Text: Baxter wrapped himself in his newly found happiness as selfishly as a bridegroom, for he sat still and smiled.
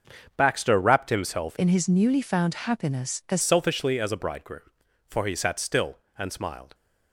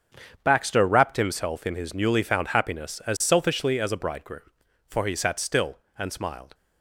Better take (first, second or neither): second